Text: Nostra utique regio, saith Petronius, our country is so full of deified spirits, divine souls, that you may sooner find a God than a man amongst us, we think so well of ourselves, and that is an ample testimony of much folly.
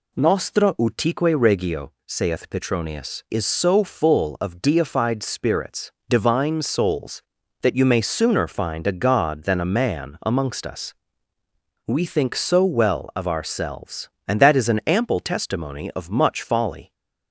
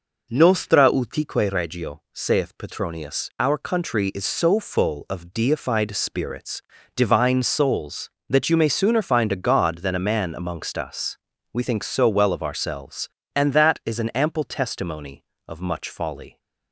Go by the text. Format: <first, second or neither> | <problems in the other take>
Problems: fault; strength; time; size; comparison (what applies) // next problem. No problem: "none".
second | skips "our country"; at 3.2 s